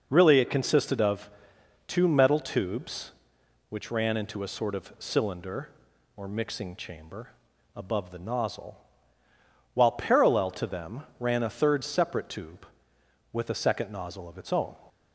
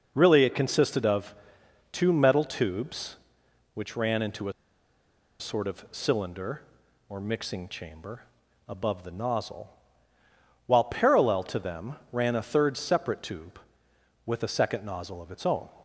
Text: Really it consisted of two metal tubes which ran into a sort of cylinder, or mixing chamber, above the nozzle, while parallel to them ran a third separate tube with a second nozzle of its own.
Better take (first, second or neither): first